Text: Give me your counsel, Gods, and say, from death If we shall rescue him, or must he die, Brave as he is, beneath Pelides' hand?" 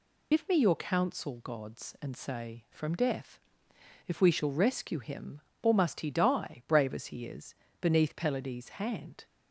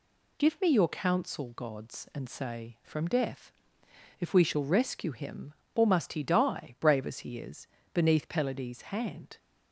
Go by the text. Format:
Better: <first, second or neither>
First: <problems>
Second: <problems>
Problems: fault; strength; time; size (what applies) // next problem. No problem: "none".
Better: second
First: loses the start of "Give"; at 0.3 s; 65 ms // pauses between "death" and "If"; noticeable; at 3.4 s; 0.66 s long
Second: pauses between "death" and "If"; noticeable; at 3.5 s; 0.66 s long